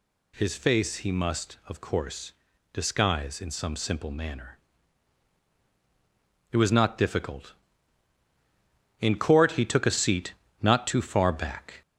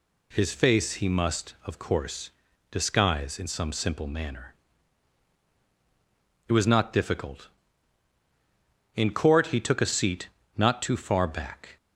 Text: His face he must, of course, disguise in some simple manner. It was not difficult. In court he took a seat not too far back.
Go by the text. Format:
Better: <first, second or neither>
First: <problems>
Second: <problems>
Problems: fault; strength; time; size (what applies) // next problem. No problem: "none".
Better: second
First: gets louder; slight; throughout; 3 dB // pauses between "seat" and "not"; slight; at 10.3 s; 0.26 s long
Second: pauses between "seat" and "not"; slight; at 10.2 s; 0.26 s long